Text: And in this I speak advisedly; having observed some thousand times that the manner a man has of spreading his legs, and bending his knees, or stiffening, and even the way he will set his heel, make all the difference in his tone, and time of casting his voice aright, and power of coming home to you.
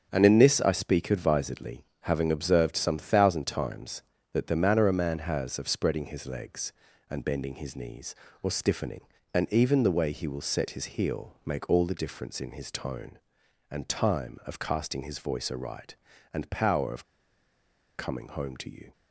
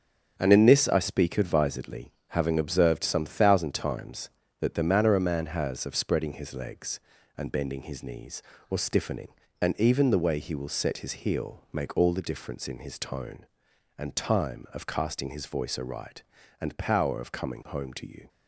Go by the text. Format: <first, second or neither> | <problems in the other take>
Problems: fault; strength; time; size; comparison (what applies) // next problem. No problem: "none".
second | starts louder than the rest; strong; until 1.1 s; 7.5 dB; strong in the second // pauses between "of" and "coming"; noticeable; at 17.0 s; 0.92 s long